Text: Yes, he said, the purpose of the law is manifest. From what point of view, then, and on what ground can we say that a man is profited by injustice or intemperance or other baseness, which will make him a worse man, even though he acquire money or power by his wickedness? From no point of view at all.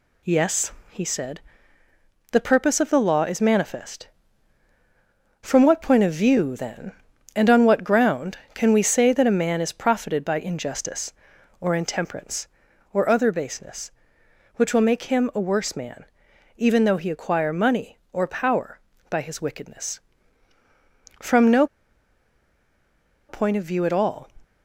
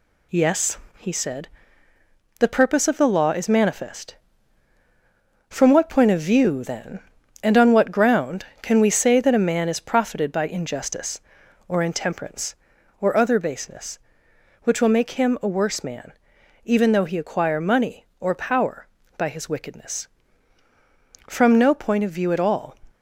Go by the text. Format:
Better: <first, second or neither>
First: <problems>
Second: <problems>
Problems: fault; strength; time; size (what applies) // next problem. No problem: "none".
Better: second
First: pauses between "no" and "point"; strong; at 21.6 s; 1.6 s long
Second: none